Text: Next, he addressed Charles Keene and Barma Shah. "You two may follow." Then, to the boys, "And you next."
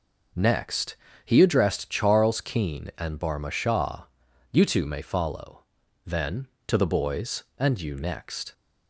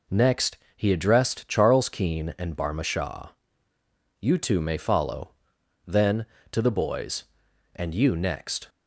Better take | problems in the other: neither | none

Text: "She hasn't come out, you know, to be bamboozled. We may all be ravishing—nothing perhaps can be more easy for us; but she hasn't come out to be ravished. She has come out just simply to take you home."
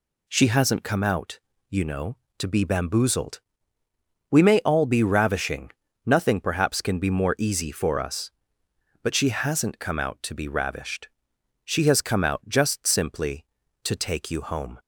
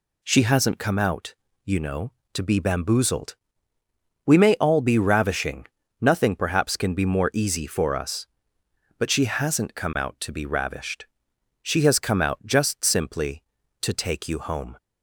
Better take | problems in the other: neither | none

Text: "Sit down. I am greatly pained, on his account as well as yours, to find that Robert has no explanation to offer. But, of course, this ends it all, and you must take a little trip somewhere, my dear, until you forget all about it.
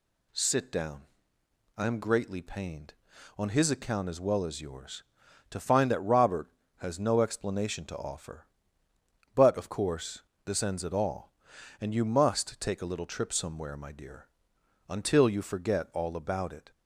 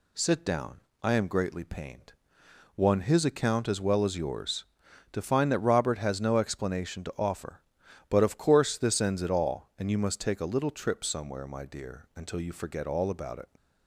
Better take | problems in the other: first | says "one" for "on"; at 2.7 s

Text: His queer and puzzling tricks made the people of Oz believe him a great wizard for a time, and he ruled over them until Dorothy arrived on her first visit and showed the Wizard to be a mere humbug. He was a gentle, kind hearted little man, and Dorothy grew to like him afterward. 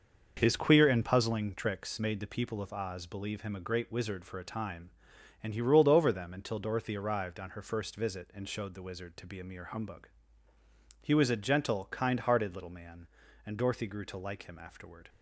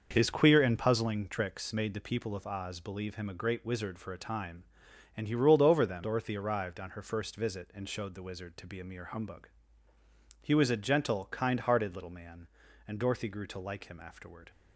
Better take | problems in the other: first | starts louder than the rest; noticeable; until 1.1 s; 6 dB; noticeable in the first // skips "until"; at 6.0 s

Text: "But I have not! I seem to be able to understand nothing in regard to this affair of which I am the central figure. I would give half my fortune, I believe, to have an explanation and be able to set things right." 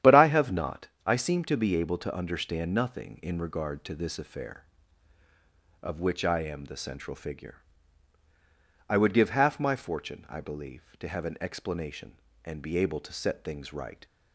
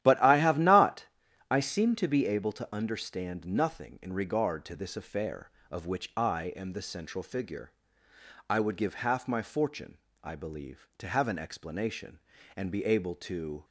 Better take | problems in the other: first | starts louder than the rest; strong; until 1.5 s; 12 dB; strong in the first // stops before "set things right"; at 13.6 s

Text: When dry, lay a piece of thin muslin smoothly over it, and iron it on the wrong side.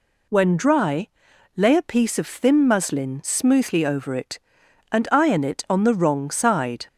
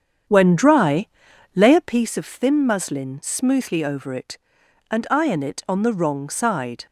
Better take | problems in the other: first | starts louder than the rest; strong; until 2.0 s; 8 dB

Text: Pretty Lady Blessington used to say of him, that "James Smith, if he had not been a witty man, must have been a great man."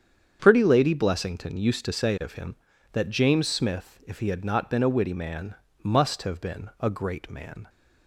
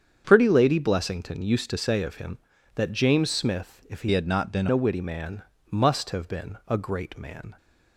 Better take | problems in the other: first | starts louder than the rest; strong; until 1.2 s; 7.5 dB; strong in the first // changes voice from "had" to "been"; from 4.1 to 4.6 s; 0.5 s long

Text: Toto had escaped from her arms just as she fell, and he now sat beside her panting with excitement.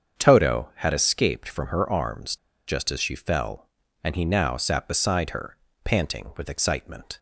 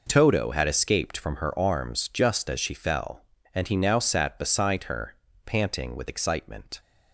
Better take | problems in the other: second | starts louder than the rest; strong; until 1.2 s; 7.5 dB // pauses between "arms" and "just"; slight; at 2.3 s; 0.30 s long // pauses between "her" and "panting"; slight; at 5.5 s; 0.28 s long; slight in the second

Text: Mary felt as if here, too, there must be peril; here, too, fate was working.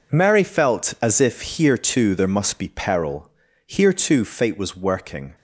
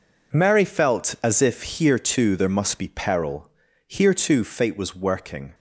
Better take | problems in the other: neither | none

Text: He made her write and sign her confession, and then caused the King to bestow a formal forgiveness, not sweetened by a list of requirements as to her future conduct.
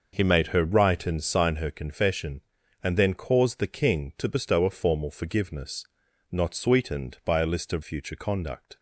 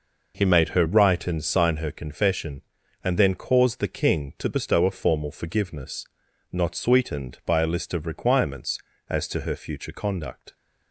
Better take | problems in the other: second | skips "requirements as to her"; at 7.8 s

